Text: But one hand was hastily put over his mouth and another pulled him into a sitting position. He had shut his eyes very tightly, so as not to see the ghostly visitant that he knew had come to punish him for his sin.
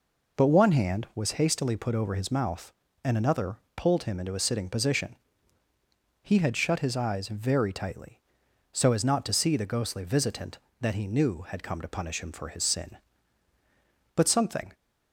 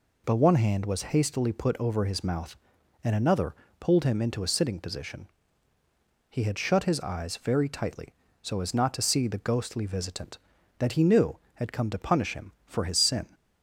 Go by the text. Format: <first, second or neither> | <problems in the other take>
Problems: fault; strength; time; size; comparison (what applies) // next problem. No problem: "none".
second | pauses between "another" and "pulled"; slight; at 3.5 s; 0.18 s long; slight in the second // goes on to say "But something"; from 14.1 s on; 0.58 s long